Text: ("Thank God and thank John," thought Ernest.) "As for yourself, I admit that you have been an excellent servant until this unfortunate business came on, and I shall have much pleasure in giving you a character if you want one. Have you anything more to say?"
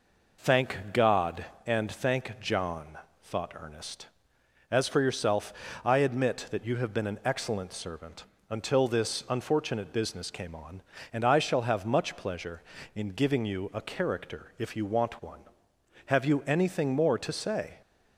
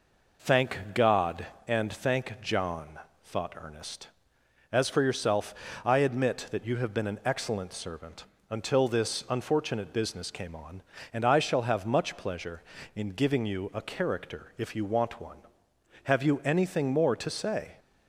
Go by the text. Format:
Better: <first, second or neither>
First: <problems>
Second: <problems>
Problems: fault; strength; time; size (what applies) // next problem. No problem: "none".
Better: neither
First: pauses between "servant" and "until"; slight; at 8.2 s; 0.26 s long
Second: pauses between "servant" and "until"; slight; at 8.2 s; 0.26 s long